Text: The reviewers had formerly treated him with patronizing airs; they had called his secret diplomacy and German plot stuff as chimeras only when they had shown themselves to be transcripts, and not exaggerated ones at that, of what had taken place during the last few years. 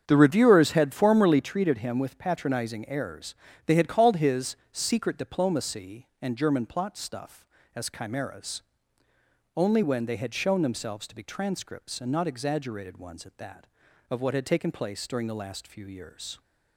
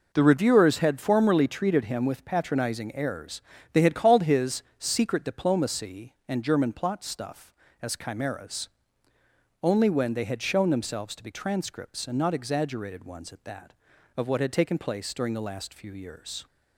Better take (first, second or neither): second